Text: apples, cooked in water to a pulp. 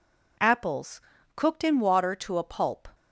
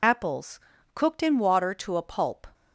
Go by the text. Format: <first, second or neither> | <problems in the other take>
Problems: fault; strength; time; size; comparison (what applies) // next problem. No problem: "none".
first | loses the start of "apples"; at 0.0 s; 45 ms